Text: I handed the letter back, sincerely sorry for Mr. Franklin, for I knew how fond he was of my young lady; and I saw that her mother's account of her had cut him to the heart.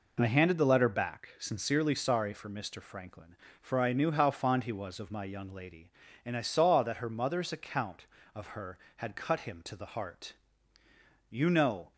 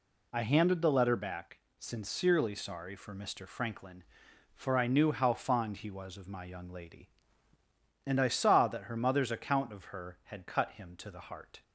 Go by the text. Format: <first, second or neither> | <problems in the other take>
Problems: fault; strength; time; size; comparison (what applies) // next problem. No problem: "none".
second | goes on to say "You know"; noticeable; from 11.2 s on; 0.64 s long